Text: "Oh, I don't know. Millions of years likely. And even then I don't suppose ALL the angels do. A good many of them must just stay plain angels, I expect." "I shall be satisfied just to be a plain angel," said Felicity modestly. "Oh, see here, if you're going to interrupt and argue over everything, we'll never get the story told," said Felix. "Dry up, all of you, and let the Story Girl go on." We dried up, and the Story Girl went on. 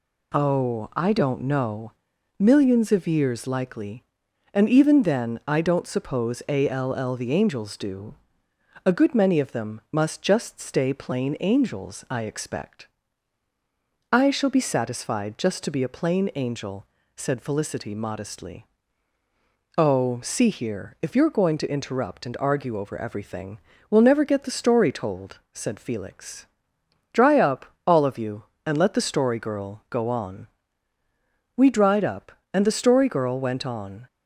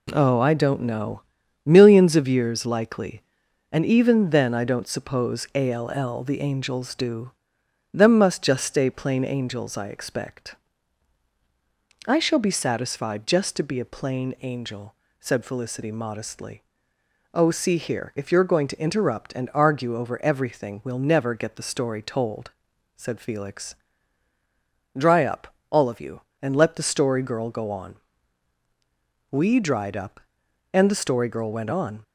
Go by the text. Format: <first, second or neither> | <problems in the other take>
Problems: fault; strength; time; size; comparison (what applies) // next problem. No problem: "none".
first | skips "A good many of"; at 7.6 s